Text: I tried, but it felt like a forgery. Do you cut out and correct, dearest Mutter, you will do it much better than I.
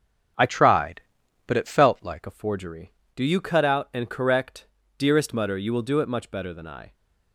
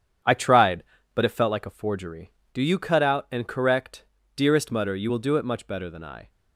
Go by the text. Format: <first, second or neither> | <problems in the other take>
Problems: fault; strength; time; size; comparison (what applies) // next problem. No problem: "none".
second | starts louder than the rest; strong; until 1.8 s; 8 dB; strong in the second // changes voice from "tried" to "like"; from 0.4 to 2.2 s; 1.8 s long